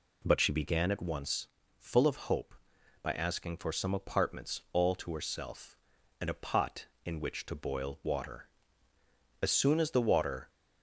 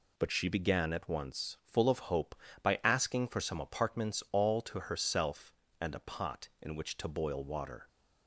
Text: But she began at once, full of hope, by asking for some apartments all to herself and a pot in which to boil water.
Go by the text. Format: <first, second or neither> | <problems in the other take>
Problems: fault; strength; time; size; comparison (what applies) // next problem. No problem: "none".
second | goes on to say "As soon as the water"; noticeable; from 9.4 s on; 1.0 s long